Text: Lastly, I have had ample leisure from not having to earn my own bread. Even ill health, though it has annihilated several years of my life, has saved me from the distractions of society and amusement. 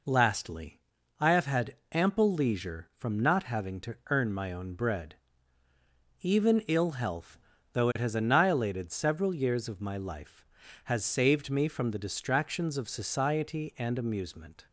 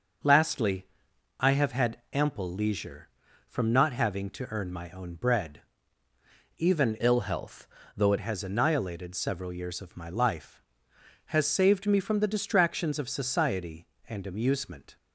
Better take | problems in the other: first | starts louder than the rest; until 1.7 s; 6 dB // pauses between "had" and "ample"; slight; at 1.9 s; 0.16 s long; slight in the first // changes voice from "ill" to "it"; from 7.0 to 8.1 s; 1.1 s long

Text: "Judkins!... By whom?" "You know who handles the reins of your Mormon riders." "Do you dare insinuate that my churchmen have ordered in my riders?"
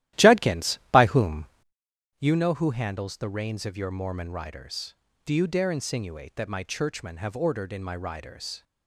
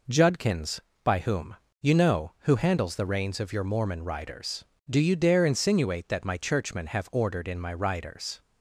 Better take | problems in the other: second | starts louder than the rest; strong; until 2.1 s; 14 dB

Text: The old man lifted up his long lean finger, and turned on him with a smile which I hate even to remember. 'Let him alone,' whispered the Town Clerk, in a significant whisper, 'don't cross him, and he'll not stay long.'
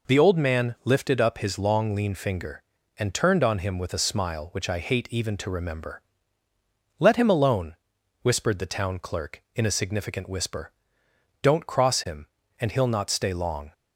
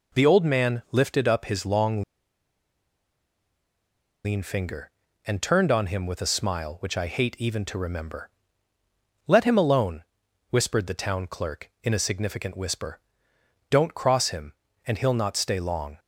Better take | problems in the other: first | pauses between "long" and "lean"; strong; at 2.0 s; 2.2 s long

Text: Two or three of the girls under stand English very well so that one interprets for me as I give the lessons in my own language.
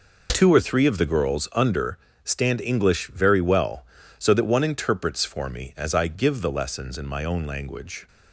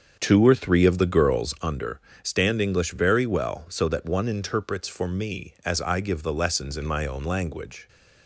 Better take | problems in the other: first | starts louder than the rest; strong; until 1.5 s; 7 dB // pauses between "under" and "stand"; slight; at 1.9 s; 0.24 s long; slight in the first

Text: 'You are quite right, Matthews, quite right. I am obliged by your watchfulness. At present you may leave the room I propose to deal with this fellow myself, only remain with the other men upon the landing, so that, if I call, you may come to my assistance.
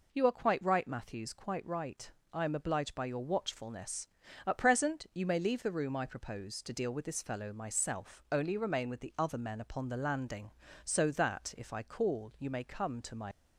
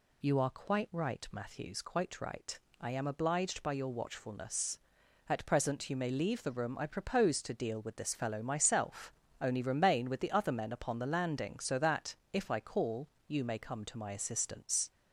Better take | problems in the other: second | stops before "assistance"; at 13.3 s

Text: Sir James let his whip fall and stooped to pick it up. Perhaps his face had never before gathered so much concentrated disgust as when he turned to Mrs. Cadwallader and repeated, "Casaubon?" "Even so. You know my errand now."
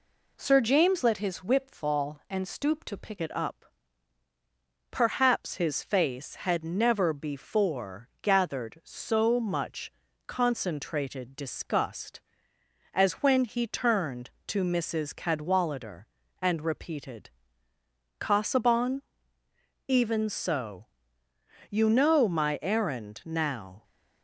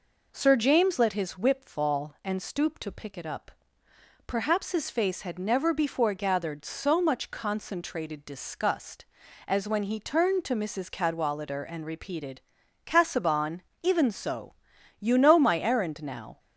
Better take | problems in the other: second | changes voice at "it"; from 3.2 s on; 20.6 s long // pauses between "much" and "concentrated"; slight; at 9.9 s; 0.34 s long

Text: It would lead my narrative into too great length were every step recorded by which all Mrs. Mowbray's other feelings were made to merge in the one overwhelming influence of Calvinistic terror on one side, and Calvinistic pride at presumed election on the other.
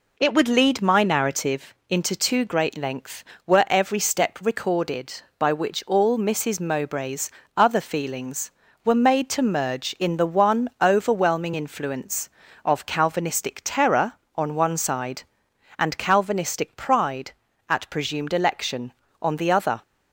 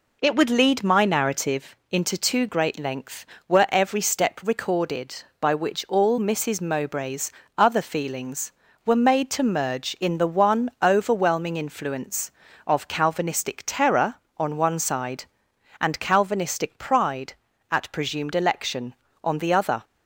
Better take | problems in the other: neither | pauses between "narrative" and "into"; slight; the same in both // pauses between "Mowbray's" and "other"; slight; the same in both

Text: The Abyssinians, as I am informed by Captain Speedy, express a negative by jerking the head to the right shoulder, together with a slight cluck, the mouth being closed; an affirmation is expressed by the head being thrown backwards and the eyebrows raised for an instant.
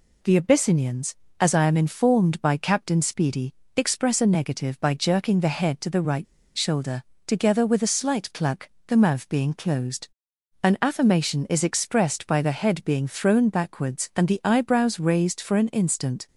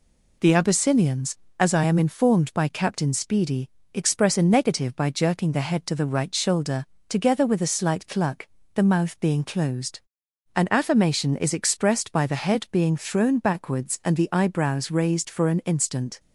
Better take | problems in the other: second | pauses between "right" and "shoulder"; slight; at 6.2 s; 0.31 s long

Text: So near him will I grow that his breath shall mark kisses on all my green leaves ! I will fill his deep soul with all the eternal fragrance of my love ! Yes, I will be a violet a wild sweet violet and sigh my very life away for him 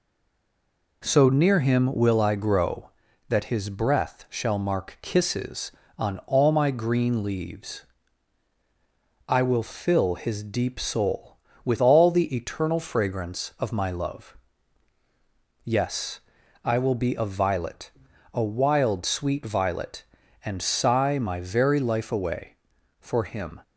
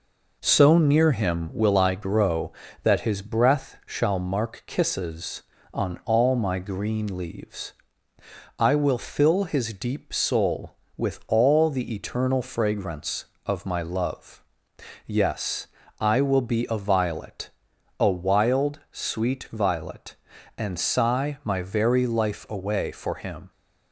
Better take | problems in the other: second | stays silent before the first word; until 1.0 s; 1.0 s long // pauses between "violet" and "a"; at 17.9 s; 0.44 s long; noticeable in the second

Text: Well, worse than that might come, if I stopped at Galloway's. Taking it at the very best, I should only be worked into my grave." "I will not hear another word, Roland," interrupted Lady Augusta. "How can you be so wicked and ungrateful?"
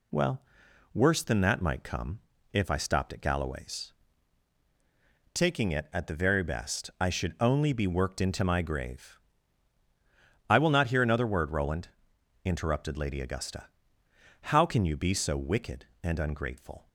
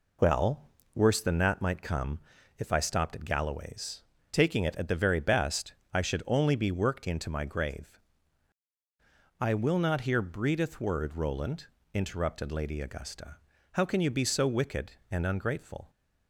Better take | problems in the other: first | says "breedeth" for "another"; at 10.1 s

